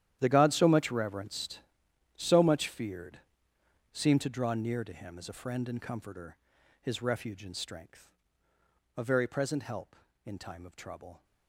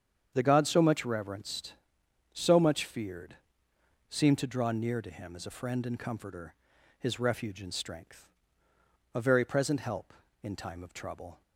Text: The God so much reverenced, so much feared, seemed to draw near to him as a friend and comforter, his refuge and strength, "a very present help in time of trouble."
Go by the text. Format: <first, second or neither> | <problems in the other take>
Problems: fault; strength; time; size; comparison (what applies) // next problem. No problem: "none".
second | gets quieter; strong; throughout; 16.5 dB // starts louder than the rest; strong; until 1.2 s; 11 dB; strong in the second